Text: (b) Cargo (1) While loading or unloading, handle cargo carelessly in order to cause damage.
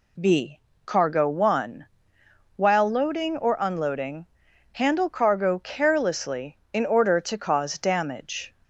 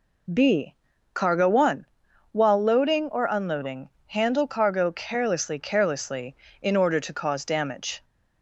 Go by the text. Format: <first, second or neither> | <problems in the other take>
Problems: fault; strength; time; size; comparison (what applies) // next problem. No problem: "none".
first | says "carelessly" twice; at 5.5 s